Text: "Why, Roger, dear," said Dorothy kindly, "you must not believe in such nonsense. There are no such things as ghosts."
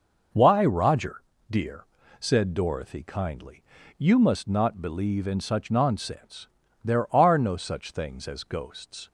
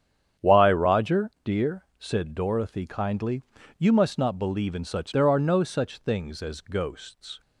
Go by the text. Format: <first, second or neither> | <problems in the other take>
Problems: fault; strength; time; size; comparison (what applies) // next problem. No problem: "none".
first | starts louder than the rest; strong; until 1.5 s; 8.5 dB // skips "nonsense"; at 5.1 s